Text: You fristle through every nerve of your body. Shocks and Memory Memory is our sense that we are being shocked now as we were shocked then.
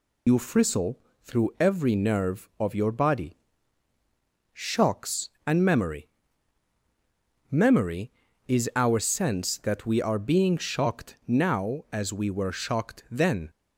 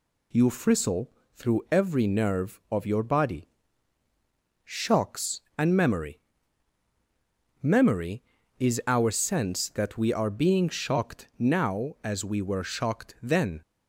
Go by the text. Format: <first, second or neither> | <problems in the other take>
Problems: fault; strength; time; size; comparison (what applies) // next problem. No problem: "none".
second | loses the start of "You"; at 0.2 s; 65 ms // pauses between "fristle" and "through"; slight; at 0.9 s; 0.26 s long; slight in the second // pauses between "Memory" and "Memory"; strong; at 6.0 s; 1.4 s long; strong in the second